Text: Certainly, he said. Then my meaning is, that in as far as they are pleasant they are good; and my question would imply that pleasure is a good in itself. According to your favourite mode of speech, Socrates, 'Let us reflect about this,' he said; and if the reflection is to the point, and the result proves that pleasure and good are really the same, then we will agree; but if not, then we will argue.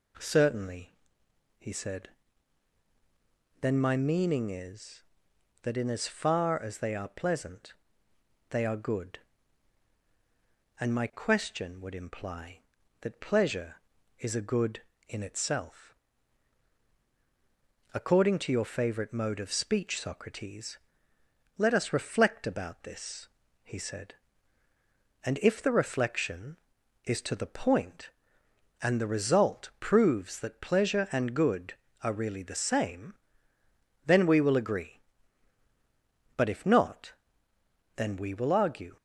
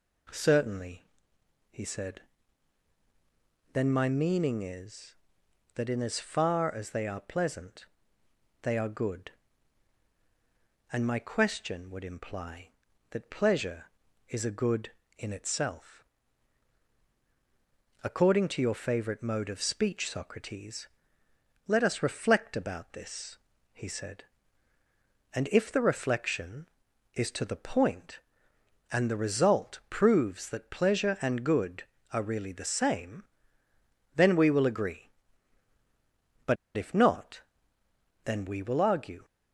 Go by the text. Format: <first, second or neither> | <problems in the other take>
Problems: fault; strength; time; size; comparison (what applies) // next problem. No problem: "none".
first | pauses between "pleasant" and "they"; noticeable; at 7.8 s; 0.76 s long; noticeable in the first // pauses between "but" and "if"; slight; at 36.5 s; 0.20 s long